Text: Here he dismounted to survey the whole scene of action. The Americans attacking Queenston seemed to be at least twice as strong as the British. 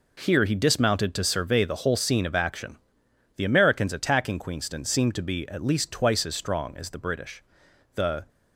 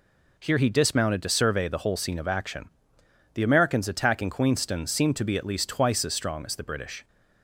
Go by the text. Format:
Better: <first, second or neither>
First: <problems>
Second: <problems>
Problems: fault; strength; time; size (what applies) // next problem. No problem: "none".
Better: second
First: goes on to say "The"; slight; from 7.9 s on; 0.34 s long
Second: none